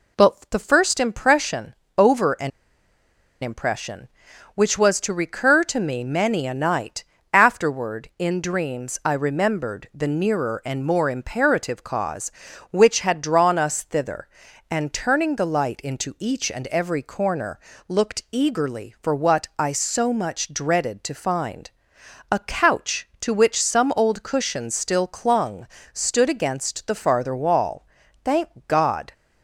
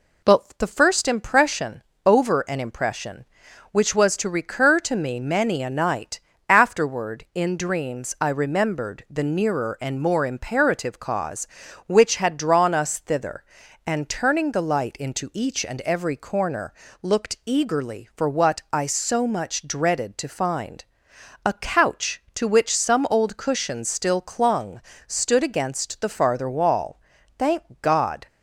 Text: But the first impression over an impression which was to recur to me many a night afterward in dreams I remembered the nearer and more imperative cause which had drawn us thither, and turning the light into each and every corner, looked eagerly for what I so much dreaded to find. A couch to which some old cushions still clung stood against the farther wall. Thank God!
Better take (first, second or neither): second